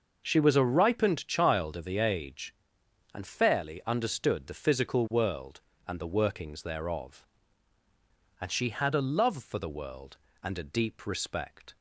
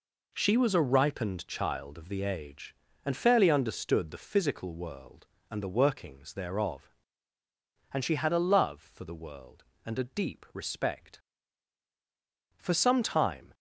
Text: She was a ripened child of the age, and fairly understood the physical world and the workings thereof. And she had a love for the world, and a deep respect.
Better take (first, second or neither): first